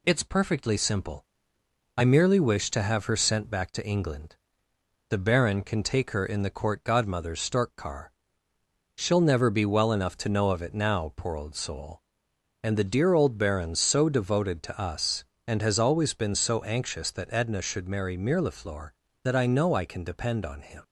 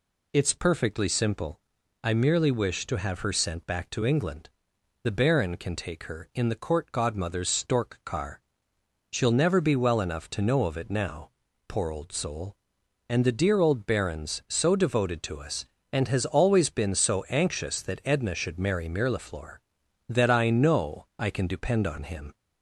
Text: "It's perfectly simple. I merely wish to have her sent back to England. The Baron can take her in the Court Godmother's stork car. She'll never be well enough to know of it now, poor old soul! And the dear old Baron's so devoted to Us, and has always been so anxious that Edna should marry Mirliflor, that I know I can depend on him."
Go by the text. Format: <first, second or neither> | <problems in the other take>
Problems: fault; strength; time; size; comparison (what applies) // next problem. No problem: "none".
neither | none